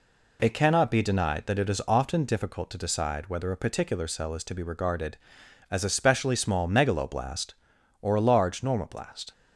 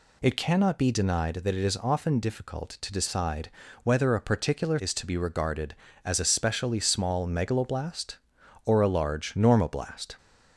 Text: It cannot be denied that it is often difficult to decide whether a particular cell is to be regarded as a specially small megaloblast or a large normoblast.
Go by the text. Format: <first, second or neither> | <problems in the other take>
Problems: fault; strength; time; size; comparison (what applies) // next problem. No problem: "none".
first | pauses between "decide" and "whether"; slight; at 3.4 s; 0.34 s long // skips "cell"; at 4.7 s